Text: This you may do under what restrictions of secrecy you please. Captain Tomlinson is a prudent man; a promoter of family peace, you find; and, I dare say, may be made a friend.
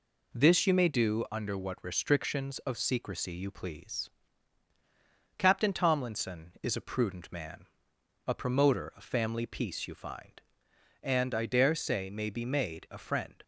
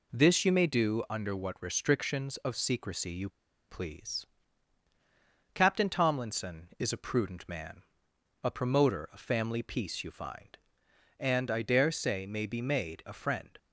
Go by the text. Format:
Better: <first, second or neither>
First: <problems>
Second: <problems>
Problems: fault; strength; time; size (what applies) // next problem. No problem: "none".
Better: first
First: none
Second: pauses between "you" and "please"; at 3.2 s; 0.41 s long